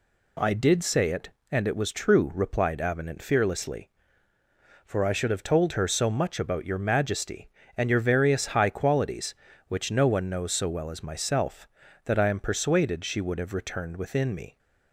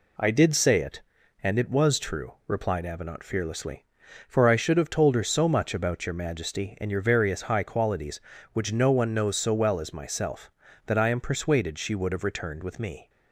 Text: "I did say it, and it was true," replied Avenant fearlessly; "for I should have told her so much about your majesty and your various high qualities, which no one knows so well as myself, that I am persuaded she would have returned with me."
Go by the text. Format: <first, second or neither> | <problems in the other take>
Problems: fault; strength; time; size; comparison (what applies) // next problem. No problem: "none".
second | says "within" for "with"; at 13.9 s